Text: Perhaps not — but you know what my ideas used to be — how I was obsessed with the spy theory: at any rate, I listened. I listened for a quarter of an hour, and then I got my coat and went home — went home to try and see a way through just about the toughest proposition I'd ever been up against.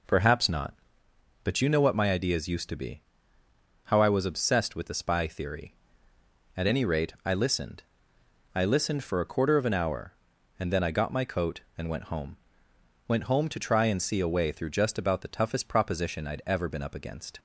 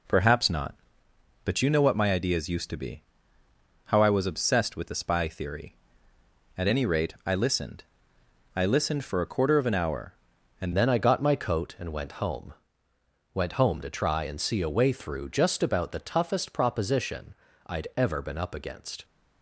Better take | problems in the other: first | changes voice at "then"; from 10.7 s on; 8.3 s long // pauses between "proposition" and "I'd"; slight; at 17.3 s; 0.32 s long

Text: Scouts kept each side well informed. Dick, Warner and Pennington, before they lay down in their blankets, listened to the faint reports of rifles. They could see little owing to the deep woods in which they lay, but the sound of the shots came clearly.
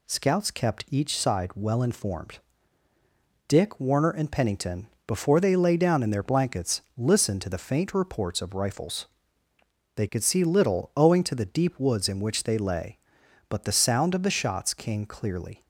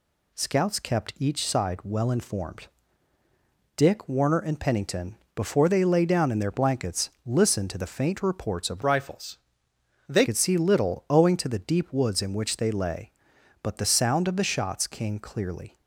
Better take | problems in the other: first | changes voice from "rifles" to "They"; from 8.8 to 10.2 s; 1.4 s long

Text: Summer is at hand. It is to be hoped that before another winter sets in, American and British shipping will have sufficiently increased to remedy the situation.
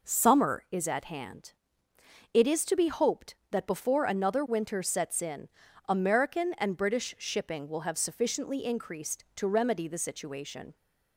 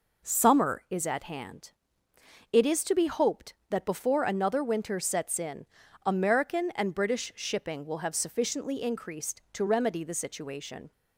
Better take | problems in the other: neither | none

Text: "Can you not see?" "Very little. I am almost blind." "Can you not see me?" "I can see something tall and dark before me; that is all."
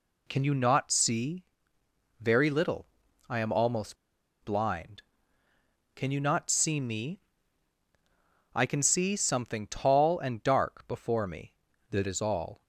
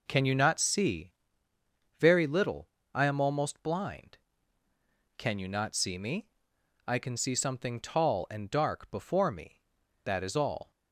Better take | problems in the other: second | pauses between "almost" and "blind"; noticeable; at 3.9 s; 0.46 s long

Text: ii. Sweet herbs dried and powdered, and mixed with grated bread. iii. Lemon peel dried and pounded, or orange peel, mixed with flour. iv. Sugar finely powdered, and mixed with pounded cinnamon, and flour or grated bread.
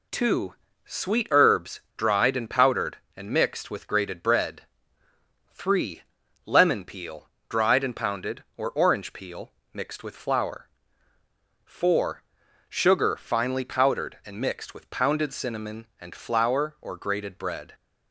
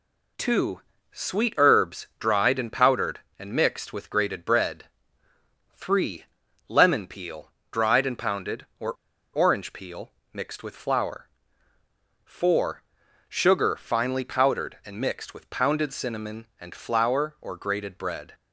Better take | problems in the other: first | pauses between "peel" and "dried"; slight; at 7.5 s; 0.18 s long; slight in the first // pauses between "or" and "orange"; at 8.9 s; 0.40 s long

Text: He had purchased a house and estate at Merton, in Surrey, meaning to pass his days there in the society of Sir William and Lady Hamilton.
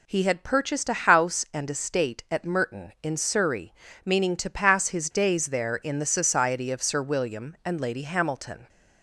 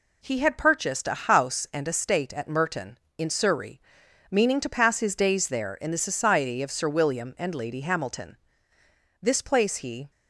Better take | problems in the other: first | goes on to say "This place he"; noticeable; from 9.2 s on; 0.88 s long

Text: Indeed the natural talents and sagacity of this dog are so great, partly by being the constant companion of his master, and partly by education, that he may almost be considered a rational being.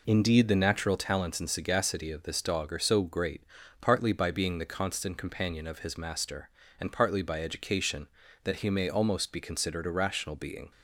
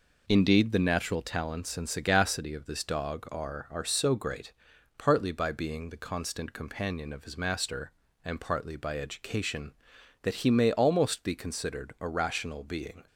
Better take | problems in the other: first | says "are" twice; at 3.7 s

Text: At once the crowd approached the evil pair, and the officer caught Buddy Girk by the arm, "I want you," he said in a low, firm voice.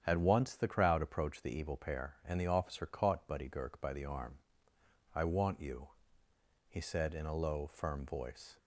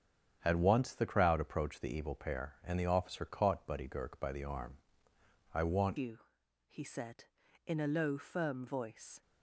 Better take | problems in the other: first | starts louder than the rest; strong; until 1.4 s; 8.5 dB; strong in the first // changes voice at "you"; from 5.9 s on; 3.3 s long

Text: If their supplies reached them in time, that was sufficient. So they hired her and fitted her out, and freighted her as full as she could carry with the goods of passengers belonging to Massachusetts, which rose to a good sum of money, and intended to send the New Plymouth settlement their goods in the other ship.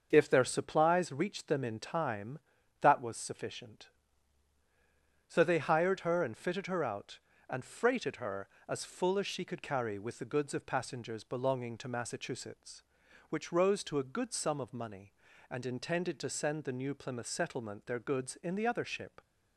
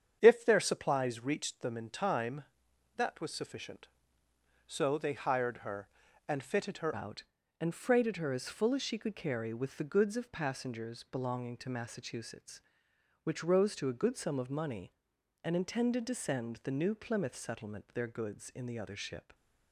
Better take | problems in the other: first | starts louder than the rest; strong; until 1.2 s; 8 dB; also in the first // changes voice at "out"; from 6.9 s on; 12.4 s long

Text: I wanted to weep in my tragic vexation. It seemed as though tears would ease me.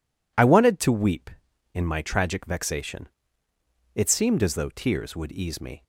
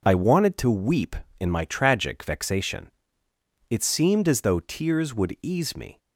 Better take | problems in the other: neither | none

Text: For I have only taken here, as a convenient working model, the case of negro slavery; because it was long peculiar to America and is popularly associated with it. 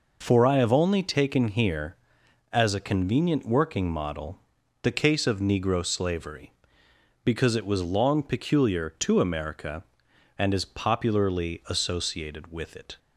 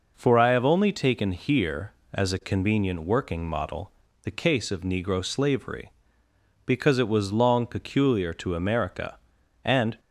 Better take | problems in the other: first | stops before "is popularly associated with it"; at 9.9 s

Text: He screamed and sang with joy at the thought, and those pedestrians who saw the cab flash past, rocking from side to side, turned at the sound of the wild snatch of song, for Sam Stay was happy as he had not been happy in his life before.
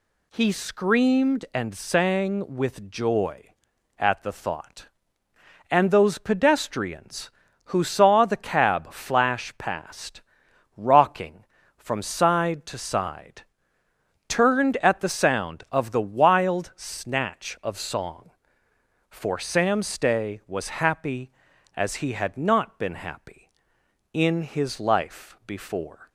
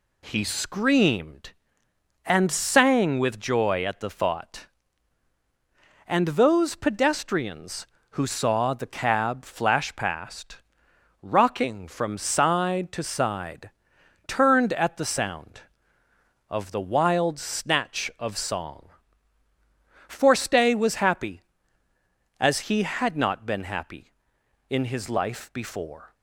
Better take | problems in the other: first | skips "Sam"; at 20.3 s

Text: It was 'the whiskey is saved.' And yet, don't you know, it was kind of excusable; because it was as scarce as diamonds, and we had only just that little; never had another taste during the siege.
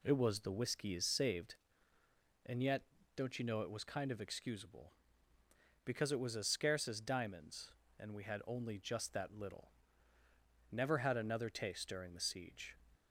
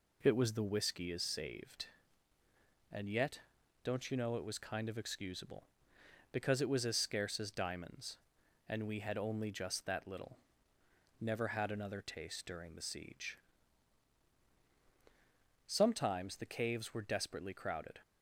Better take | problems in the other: first | goes on to say "Sometimes the caves were desperately crowded"; strong; from 15.6 s on; 2.3 s long

